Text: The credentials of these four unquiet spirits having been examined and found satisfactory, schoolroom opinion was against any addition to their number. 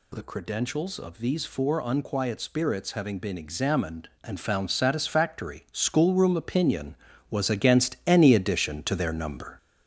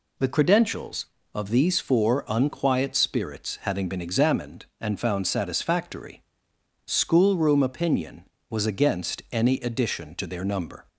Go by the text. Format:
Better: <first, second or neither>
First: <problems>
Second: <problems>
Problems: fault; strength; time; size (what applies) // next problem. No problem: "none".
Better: second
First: gets louder; noticeable; throughout; 5.5 dB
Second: none